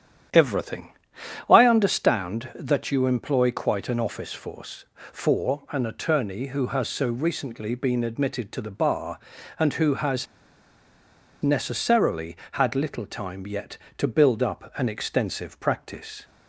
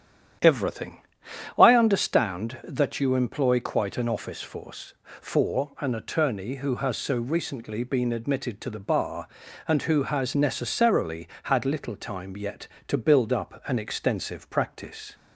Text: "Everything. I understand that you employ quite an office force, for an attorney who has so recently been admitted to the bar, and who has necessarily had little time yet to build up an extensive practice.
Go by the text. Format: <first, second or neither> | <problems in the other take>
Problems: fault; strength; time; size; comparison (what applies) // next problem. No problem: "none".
second | starts louder than the rest; strong; until 1.8 s; 10 dB; strong in the second // pauses between "has" and "necessarily"; at 10.2 s; 1.1 s long